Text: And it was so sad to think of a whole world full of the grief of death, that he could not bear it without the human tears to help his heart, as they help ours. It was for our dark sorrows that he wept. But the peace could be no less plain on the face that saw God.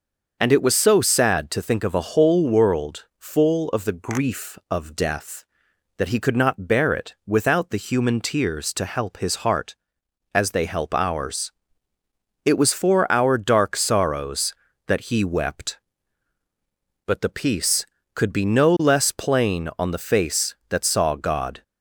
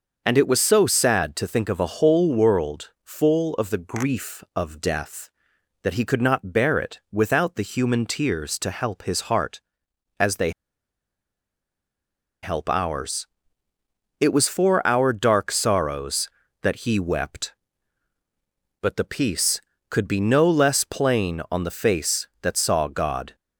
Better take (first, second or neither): first